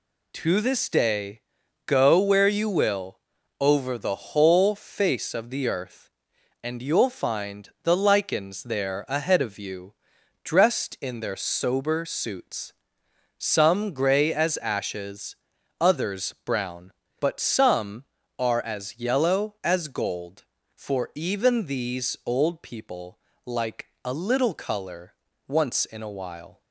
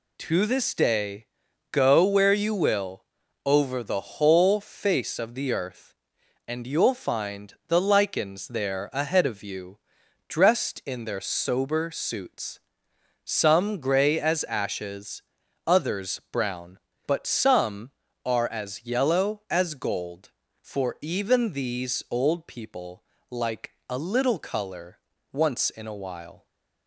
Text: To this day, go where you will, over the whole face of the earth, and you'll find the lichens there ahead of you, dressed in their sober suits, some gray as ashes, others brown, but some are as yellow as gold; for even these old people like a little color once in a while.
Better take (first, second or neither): neither